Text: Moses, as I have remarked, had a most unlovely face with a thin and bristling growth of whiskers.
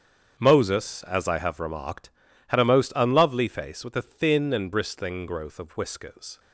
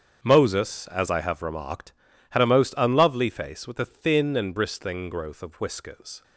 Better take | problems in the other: neither | starts louder than the rest; strong; the same in both

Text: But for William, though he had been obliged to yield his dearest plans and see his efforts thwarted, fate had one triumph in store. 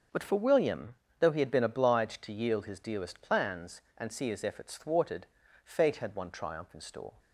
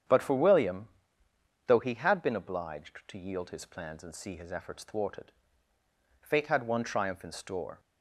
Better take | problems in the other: first | starts louder than the rest; strong; until 1.8 s; 8.5 dB; also in the first // skips "dearest"; at 3.6 s

